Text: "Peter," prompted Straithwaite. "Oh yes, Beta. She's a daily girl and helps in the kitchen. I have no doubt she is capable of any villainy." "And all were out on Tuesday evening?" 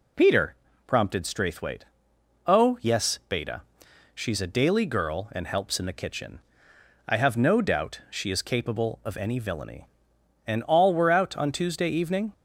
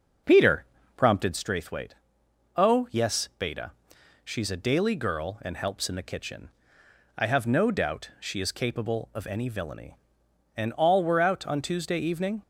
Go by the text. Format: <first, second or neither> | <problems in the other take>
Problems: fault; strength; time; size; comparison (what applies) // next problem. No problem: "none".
first | starts louder than the rest; noticeable; until 1.5 s; 6 dB